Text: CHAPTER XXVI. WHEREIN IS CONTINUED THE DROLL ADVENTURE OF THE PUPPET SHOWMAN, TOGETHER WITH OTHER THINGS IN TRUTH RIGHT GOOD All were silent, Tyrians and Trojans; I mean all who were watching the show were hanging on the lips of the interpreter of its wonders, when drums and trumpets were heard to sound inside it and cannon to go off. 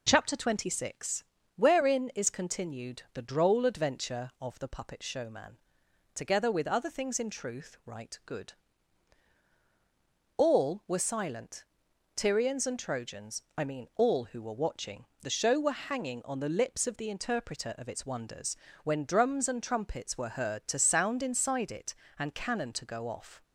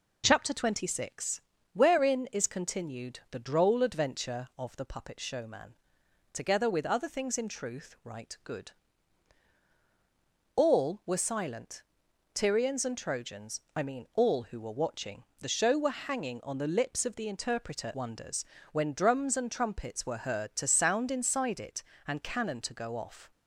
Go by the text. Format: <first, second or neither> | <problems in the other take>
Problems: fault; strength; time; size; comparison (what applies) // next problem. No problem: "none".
first | pauses between "GOOD" and "All"; strong; at 8.7 s; 1.8 s long; strong in the first // pauses between "watching" and "the"; slight; at 15.2 s; 0.16 s long; slight in the first // skips "of its"; at 17.9 s